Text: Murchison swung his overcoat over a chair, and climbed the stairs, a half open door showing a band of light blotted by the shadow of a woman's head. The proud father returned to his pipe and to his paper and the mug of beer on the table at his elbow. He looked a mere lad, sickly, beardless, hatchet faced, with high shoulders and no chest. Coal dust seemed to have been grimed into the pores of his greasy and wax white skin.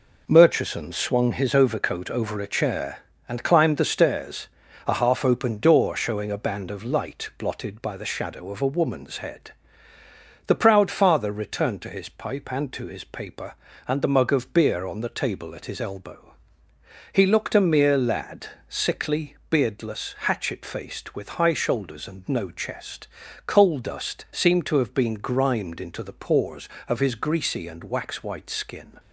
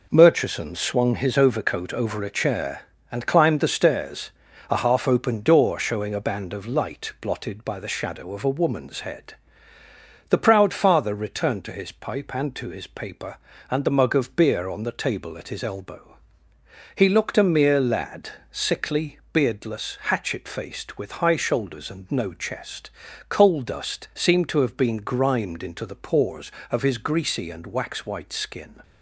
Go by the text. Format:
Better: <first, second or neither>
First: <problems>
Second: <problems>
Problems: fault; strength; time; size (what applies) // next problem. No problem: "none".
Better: neither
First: none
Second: none